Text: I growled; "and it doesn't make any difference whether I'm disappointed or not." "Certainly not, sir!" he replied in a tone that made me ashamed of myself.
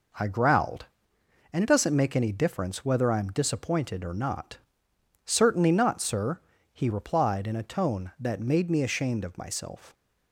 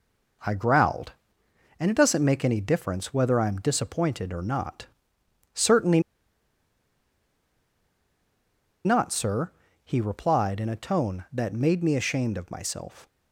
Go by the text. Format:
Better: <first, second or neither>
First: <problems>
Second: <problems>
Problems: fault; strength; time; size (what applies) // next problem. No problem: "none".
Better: first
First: none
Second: pauses between "Certainly" and "not"; strong; at 5.9 s; 2.8 s long